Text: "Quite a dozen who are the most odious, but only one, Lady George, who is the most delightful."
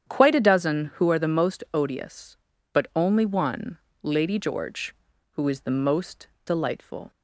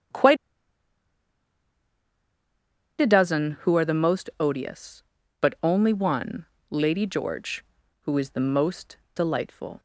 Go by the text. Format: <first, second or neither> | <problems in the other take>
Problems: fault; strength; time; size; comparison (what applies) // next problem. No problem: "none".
first | starts louder than the rest; strong; until 3.8 s; 9 dB; strong in the first // pauses between "Quite" and "a"; strong; at 0.3 s; 2.6 s long // pauses between "most" and "delightful"; slight; at 8.9 s; 0.18 s long; slight in the first